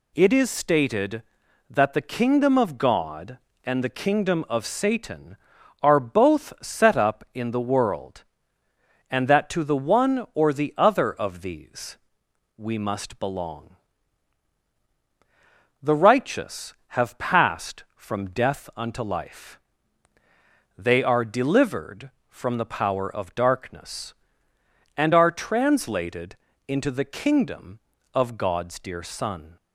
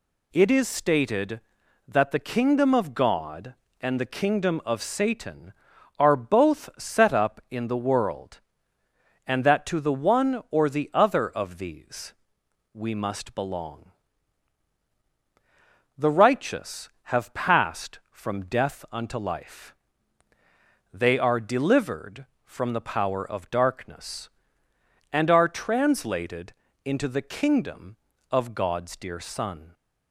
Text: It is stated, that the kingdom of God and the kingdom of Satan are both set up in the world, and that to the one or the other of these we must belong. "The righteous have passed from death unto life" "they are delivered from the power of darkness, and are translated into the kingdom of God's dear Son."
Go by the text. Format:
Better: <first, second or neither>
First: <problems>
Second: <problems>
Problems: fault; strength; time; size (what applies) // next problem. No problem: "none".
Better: neither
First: pauses between "these" and "we"; noticeable; at 11.9 s; 0.60 s long // pauses between "life" and "they"; at 19.5 s; 1.2 s long // pauses between "translated" and "into"; slight; at 26.3 s; 0.32 s long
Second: pauses between "these" and "we"; noticeable; at 12.1 s; 0.60 s long // pauses between "life" and "they"; at 19.7 s; 1.2 s long // pauses between "translated" and "into"; slight; at 26.5 s; 0.32 s long